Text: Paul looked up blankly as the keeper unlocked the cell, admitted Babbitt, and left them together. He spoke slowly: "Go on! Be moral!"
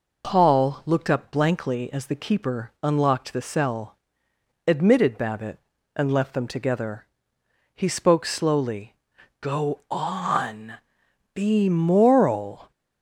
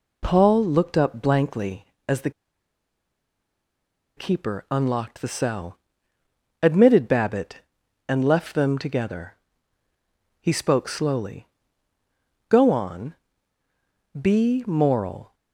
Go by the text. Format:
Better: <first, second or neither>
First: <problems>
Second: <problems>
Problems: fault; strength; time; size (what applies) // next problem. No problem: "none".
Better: first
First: none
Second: pauses between "the" and "keeper"; strong; at 2.2 s; 1.8 s long